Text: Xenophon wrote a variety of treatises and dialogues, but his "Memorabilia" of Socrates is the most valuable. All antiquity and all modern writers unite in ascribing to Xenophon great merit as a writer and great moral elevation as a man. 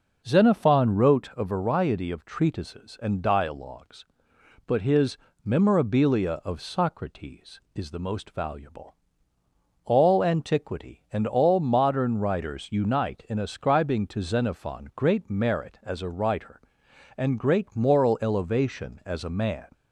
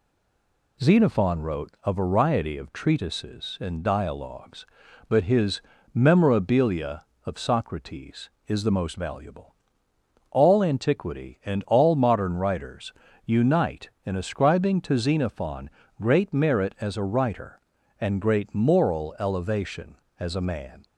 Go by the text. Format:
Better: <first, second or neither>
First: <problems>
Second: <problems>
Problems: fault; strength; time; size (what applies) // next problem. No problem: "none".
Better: first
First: pauses between "his" and "Memorabilia"; slight; at 5.1 s; 0.26 s long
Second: stays silent before the first word; slight; until 0.7 s; 0.7 s long // pauses between "his" and "Memorabilia"; slight; at 5.5 s; 0.32 s long // pauses between "writers" and "unite"; slight; at 12.9 s; 0.32 s long // pauses between "Xenophon" and "great"; slight; at 15.7 s; 0.30 s long